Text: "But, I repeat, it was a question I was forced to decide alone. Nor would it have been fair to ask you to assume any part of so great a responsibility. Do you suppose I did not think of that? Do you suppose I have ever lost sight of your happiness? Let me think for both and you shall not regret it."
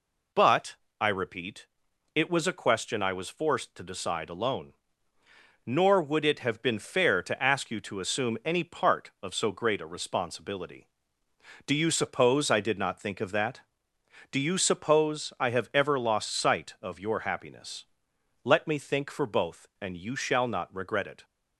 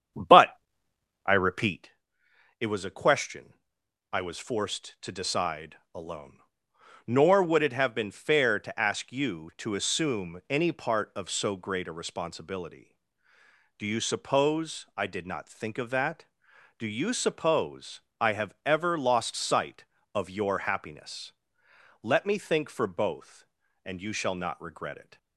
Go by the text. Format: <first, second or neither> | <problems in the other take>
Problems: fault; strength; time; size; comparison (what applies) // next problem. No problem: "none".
first | starts louder than the rest; strong; until 1.9 s; 8.5 dB // pauses between "question" and "I"; noticeable; at 3.5 s; 0.58 s long // pauses between "suppose" and "I"; slight; at 17.9 s; 0.22 s long